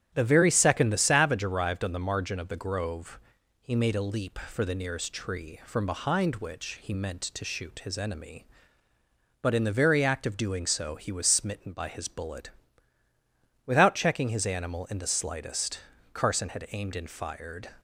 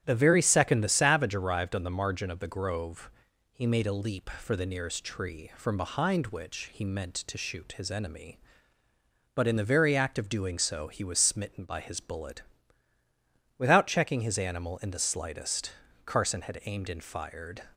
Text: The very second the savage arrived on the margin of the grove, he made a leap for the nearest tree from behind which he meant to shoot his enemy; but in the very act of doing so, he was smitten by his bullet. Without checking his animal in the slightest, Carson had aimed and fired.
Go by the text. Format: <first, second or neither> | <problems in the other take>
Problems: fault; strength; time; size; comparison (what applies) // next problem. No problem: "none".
neither | starts louder than the rest; strong; the same in both